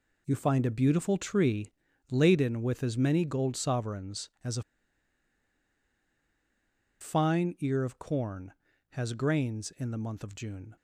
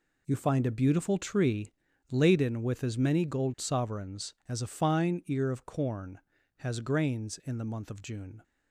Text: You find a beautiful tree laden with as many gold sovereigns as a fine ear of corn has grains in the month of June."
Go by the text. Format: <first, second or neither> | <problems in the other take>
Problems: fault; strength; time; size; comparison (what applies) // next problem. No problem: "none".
second | pauses between "tree" and "laden"; at 1.7 s; 0.40 s long; also in the second // pauses between "a" and "fine"; strong; at 4.6 s; 2.3 s long